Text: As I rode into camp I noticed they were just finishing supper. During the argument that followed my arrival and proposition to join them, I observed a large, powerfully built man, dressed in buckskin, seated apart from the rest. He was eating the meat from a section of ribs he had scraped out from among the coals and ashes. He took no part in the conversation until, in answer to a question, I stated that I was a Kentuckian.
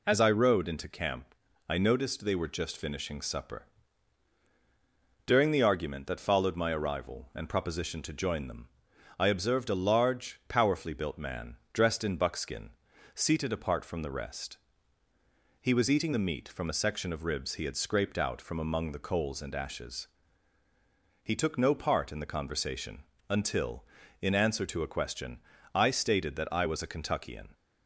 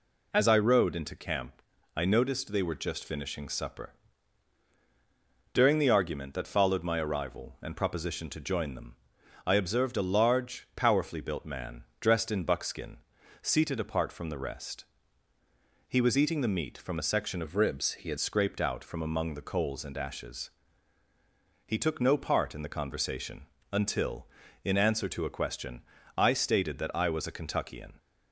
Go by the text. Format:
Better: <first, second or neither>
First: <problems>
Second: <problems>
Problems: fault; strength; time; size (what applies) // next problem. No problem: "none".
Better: first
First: pauses between "camp" and "I"; slight; at 1.3 s; 0.36 s long // pauses between "conversation" and "until"; slight; at 23.0 s; 0.26 s long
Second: pauses between "camp" and "I"; slight; at 1.6 s; 0.36 s long // changes voice from "of" to "had"; from 17.4 to 18.1 s; 0.7 s long // pauses between "conversation" and "until"; slight; at 23.4 s; 0.26 s long